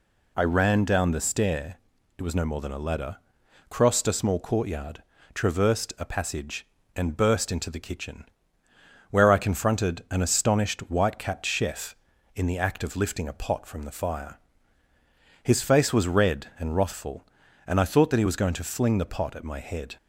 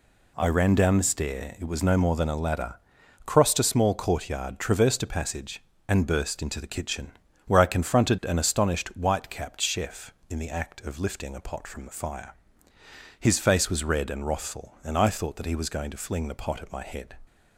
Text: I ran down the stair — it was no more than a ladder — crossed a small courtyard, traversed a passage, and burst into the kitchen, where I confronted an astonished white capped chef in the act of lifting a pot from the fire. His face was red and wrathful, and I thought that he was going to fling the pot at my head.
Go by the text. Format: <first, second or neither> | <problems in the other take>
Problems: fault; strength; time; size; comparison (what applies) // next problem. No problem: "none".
neither | none